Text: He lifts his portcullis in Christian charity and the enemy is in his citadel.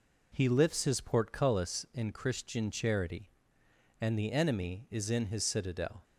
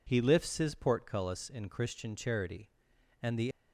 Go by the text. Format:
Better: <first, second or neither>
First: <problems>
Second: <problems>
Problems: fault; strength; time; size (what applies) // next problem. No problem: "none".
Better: first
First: none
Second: stops before "enemy is in his citadel"; at 3.5 s